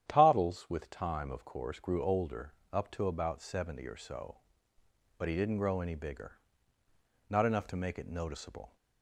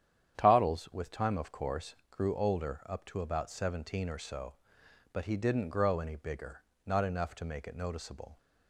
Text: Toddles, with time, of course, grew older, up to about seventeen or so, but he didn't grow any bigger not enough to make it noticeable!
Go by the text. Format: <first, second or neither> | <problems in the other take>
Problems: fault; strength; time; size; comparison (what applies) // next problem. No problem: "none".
second | starts louder than the rest; strong; until 1.0 s; 10.5 dB; strong in the second // says "seventy" for "seventeen"; at 3.4 s // pauses between "bigger" and "not"; noticeable; at 6.3 s; 0.90 s long; slight in the second